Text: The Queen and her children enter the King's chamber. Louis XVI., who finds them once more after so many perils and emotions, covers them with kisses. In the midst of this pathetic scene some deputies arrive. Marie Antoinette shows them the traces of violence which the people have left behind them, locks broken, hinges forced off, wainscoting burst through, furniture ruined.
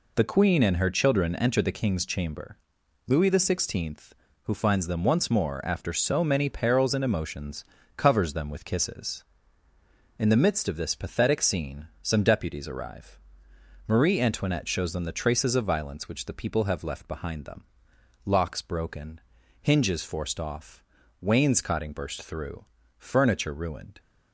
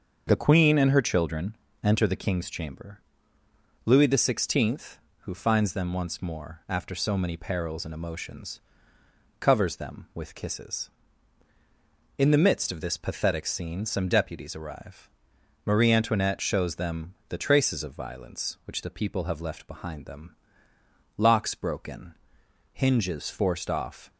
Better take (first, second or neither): first